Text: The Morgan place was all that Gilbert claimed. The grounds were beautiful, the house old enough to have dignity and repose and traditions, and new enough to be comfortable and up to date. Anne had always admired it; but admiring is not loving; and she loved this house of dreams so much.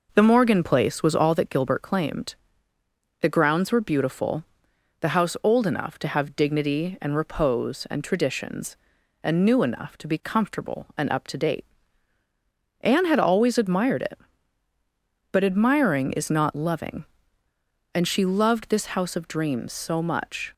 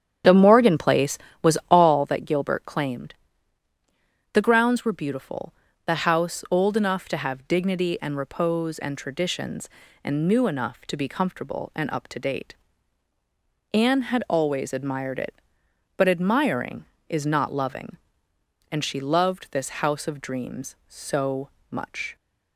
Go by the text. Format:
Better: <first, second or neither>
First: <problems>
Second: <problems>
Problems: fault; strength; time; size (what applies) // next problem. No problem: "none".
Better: first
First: none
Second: starts louder than the rest; strong; until 2.1 s; 9 dB // pauses between "so" and "much"; slight; at 21.4 s; 0.20 s long